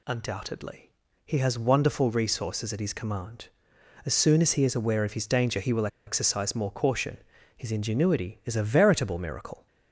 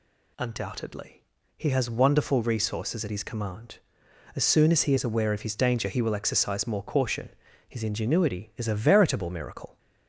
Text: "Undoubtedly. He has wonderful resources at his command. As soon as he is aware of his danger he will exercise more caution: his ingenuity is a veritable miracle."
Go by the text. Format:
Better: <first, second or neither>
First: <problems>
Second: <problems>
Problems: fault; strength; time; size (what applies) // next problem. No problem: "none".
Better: second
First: pauses between "will" and "exercise"; slight; at 5.8 s; 0.20 s long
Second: none